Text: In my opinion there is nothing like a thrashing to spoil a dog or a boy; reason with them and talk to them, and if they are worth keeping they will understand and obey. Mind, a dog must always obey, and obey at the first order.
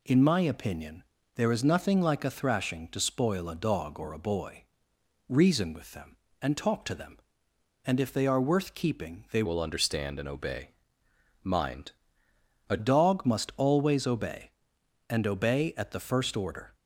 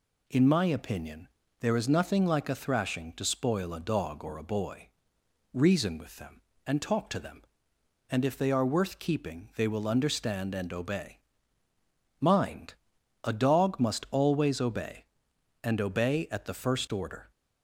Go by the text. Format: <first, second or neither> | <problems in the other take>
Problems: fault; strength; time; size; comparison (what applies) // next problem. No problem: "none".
second | pauses between "opinion" and "there"; slight; at 1.0 s; 0.32 s long; slight in the second // changes voice from "will" to "a"; from 9.4 to 12.7 s; 3.3 s long